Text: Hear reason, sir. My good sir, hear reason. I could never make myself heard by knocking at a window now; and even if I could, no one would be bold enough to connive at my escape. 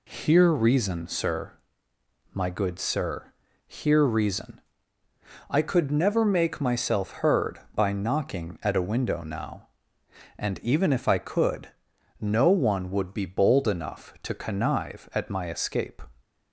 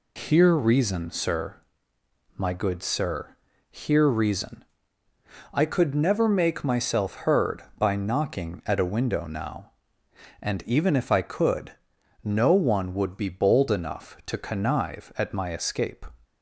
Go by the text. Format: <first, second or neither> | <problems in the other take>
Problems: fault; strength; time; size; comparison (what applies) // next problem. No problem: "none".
first | loses the start of "Hear"; at 0.1 s; 60 ms